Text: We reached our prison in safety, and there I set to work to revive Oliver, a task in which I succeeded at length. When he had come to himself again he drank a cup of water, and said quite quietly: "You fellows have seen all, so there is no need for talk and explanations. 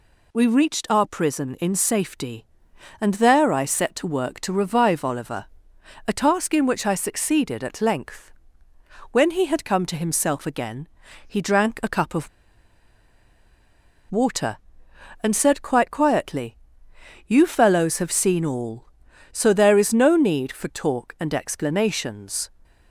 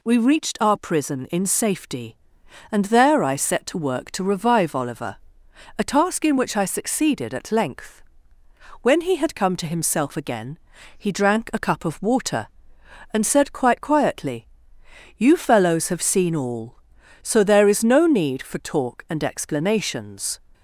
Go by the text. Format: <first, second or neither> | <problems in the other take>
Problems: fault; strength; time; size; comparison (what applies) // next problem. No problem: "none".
second | pauses between "again" and "he"; at 10.8 s; 0.40 s long; also in the second // pauses between "of" and "water"; strong; at 12.2 s; 1.8 s long